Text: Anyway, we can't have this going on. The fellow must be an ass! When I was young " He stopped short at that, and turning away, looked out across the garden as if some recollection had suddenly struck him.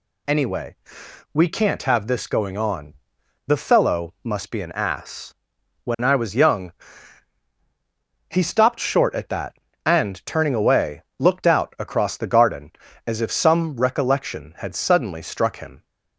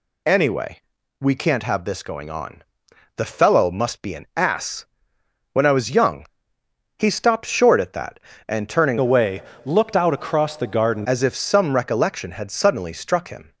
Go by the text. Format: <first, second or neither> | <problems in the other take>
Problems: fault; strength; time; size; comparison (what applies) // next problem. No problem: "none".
first | changes voice from "away" to "garden"; from 8.9 to 11.0 s; 2.1 s long